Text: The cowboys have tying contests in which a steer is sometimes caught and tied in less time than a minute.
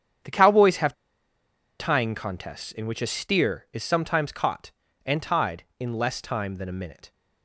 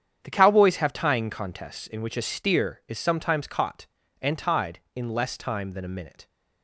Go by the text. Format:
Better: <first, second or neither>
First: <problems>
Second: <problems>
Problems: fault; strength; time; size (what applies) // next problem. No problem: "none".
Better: second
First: starts louder than the rest; strong; until 2.0 s; 8 dB // pauses between "have" and "tying"; noticeable; at 0.9 s; 0.85 s long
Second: starts louder than the rest; strong; until 1.2 s; 8 dB